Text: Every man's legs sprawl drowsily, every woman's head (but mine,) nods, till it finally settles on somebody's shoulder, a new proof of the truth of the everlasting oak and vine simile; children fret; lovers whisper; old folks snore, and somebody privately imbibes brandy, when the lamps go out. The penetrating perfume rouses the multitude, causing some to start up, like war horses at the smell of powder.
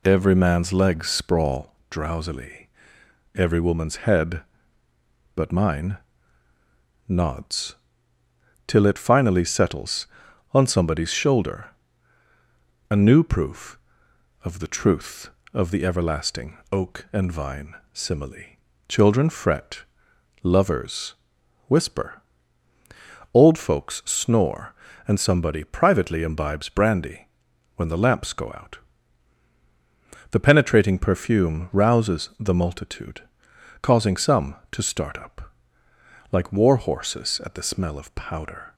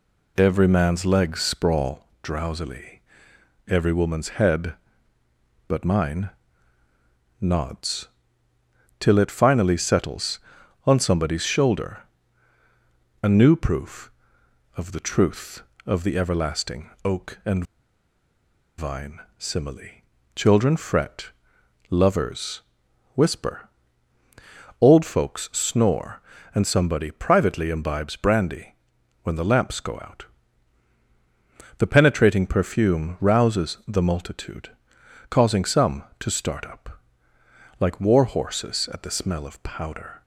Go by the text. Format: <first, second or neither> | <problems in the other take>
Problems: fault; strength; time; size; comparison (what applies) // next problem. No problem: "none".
first | pauses between "everlasting" and "oak"; slight; at 16.8 s; 0.16 s long; slight in the first // pauses between "and" and "vine"; at 17.6 s; 1.1 s long // pauses between "vine" and "simile"; slight; at 19.1 s; 0.20 s long; slight in the first // pauses between "lovers" and "whisper"; noticeable; at 22.6 s; 0.54 s long; noticeable in the first